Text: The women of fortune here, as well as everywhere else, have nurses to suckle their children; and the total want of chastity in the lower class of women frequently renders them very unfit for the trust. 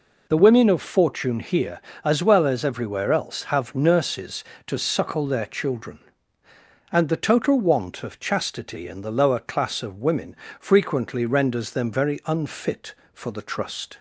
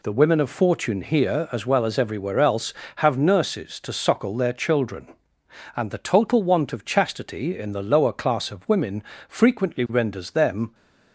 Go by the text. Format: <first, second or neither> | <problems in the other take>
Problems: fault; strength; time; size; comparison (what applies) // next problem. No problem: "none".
first | pauses between "women" and "frequently"; slight; at 9.0 s; 0.24 s long; slight in the first // stops before "very unfit for the trust"; at 10.7 s